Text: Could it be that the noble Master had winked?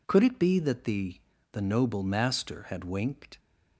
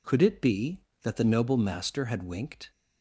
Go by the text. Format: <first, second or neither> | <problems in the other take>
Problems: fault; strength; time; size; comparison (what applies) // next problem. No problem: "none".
second | says "the" twice; at 1.5 s